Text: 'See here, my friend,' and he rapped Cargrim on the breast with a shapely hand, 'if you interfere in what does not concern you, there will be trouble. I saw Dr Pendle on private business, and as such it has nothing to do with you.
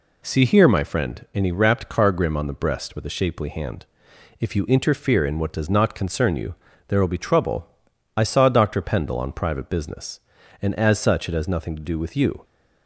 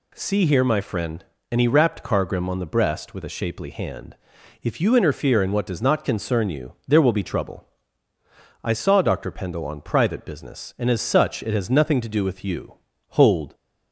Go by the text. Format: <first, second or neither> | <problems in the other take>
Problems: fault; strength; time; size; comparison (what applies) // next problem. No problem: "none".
first | goes on to say "Hold"; slight; from 13.1 s on; 0.42 s long